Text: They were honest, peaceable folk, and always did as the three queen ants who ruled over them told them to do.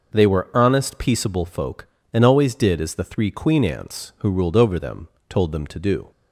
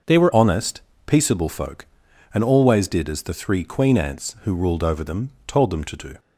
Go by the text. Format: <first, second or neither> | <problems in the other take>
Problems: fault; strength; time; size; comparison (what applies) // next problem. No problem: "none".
first | changes voice at "honest"; from 0.3 s on; 5.8 s long // pauses between "them" and "told"; slight; at 5.3 s; 0.16 s long; slight in the first